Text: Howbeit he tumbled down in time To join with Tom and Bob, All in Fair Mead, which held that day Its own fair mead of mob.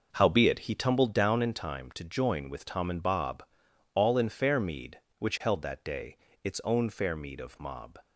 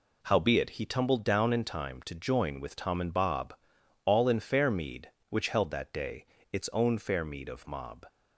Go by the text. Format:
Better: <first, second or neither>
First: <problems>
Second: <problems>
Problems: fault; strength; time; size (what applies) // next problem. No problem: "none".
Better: second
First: starts louder than the rest; noticeable; until 1.4 s; 5.5 dB // pauses between "day" and "Its"; slight; at 6.1 s; 0.26 s long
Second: pauses between "day" and "Its"; slight; at 6.2 s; 0.26 s long